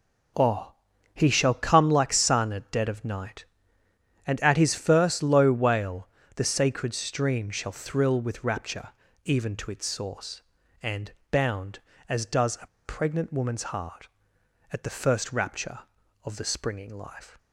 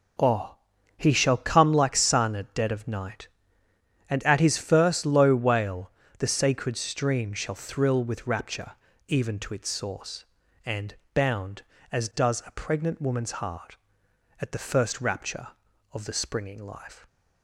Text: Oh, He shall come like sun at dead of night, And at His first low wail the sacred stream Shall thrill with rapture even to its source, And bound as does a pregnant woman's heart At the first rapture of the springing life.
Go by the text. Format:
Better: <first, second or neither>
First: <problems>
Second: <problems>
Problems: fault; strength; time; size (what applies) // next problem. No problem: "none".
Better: second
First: pauses between "wail" and "the"; slight; at 6.0 s; 0.28 s long // pauses between "rapture" and "even"; slight; at 8.8 s; 0.36 s long // pauses between "And" and "bound"; slight; at 11.1 s; 0.18 s long // pauses between "a" and "pregnant"; slight; at 12.6 s; 0.18 s long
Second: pauses between "wail" and "the"; slight; at 5.9 s; 0.28 s long // pauses between "rapture" and "even"; slight; at 8.7 s; 0.36 s long // pauses between "And" and "bound"; slight; at 10.9 s; 0.18 s long